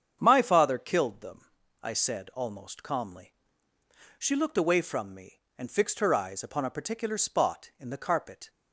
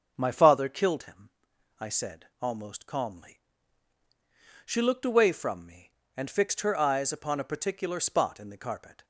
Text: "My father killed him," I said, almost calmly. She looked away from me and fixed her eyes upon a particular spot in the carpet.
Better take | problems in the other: second | starts louder than the rest; strong; until 1.2 s; 8 dB; also in the second // says "them" for "him"; at 1.2 s

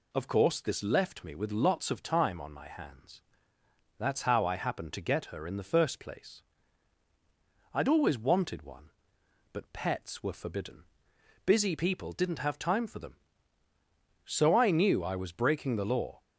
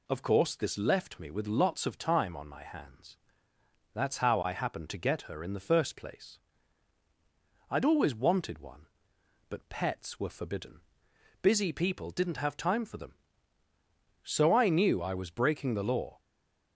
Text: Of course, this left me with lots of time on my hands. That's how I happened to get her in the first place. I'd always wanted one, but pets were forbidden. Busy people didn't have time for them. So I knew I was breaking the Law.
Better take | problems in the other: first | stays silent after the last word; slight; from 16.1 s on; 0.6 s long

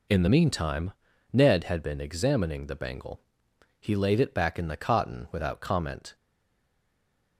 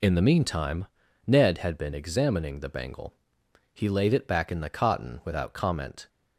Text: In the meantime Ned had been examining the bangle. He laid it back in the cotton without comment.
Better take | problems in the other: second | pauses between "meantime" and "Ned"; at 0.9 s; 0.42 s long; also in the second // stays silent after the last word; noticeable; from 6.1 s on; 1.2 s long

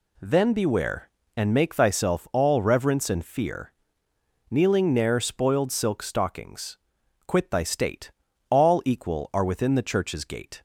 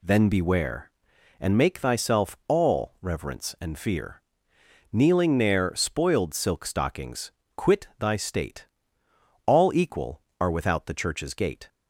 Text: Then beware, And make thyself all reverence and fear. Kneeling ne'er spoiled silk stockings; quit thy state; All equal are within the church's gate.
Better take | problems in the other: first | says "without" for "within"; at 10.5 s

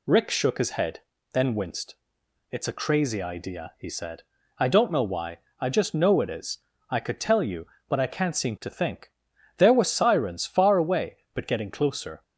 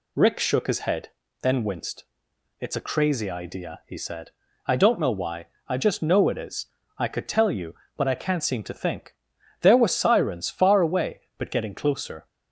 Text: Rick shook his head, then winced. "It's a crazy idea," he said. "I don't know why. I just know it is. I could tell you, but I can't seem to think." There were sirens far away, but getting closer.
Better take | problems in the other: neither | none

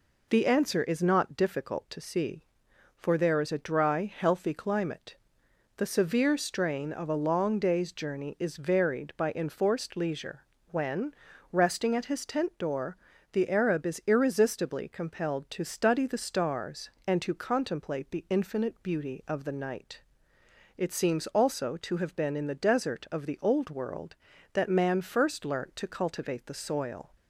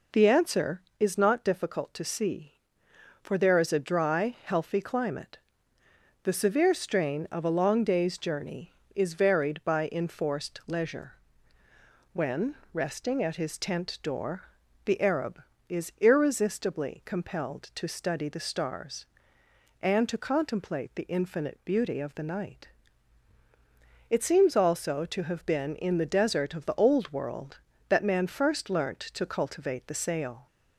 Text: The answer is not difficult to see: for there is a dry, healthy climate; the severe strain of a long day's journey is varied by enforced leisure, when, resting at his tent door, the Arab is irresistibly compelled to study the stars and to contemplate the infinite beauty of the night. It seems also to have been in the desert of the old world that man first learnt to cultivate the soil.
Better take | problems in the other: first | says "sail" for "soil"; at 29.9 s

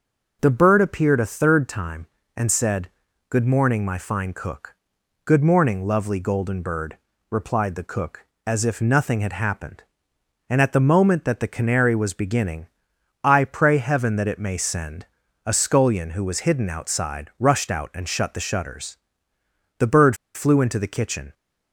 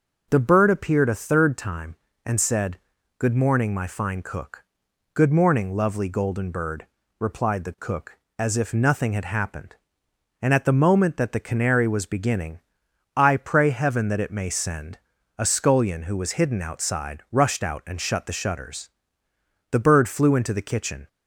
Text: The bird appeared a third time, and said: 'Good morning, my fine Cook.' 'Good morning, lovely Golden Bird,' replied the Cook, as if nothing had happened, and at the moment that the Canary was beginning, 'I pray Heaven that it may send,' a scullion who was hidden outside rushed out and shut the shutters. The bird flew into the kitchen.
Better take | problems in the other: second | pauses between "bird" and "flew"; slight; at 20.1 s; 0.19 s long

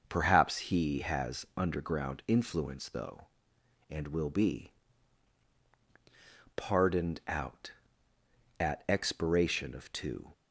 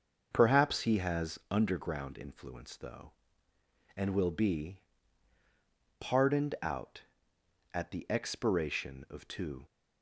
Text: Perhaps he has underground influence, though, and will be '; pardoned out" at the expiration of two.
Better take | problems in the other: second | starts louder than the rest; until 1.0 s; 7 dB; also in the second // skips "the"; at 8.8 s

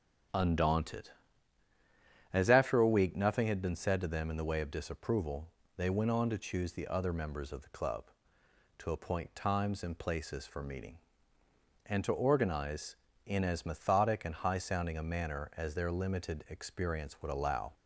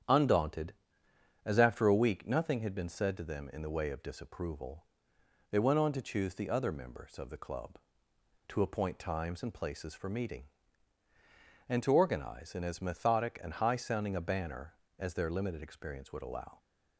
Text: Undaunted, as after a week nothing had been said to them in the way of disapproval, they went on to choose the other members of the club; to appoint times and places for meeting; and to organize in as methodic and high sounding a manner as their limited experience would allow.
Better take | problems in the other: first | starts louder than the rest; strong; until 1.8 s; 9 dB; strong in the first // says "banner" for "manner"; at 14.2 s

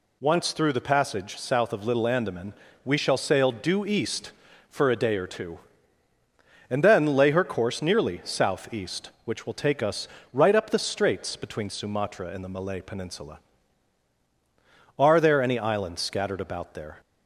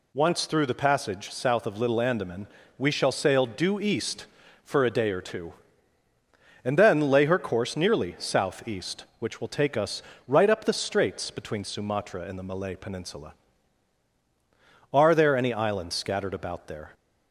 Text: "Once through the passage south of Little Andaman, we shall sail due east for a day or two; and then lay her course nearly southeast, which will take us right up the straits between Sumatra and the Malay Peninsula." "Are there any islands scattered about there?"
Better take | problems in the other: neither | pauses between "us" and "right"; slight; the same in both

